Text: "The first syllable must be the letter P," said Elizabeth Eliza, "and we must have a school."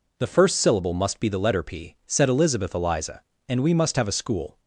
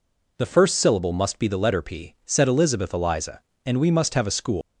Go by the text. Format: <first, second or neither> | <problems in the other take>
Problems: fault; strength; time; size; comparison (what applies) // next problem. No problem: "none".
first | leaves "school" unfinished; at 4.6 s; 175 ms